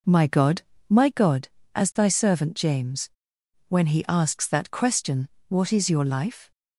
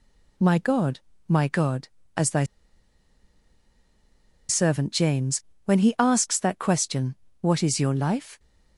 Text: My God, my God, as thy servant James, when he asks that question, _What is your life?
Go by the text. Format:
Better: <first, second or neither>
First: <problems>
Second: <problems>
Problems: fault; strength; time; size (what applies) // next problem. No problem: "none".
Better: first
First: none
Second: pauses between "thy" and "servant"; strong; at 2.4 s; 2.0 s long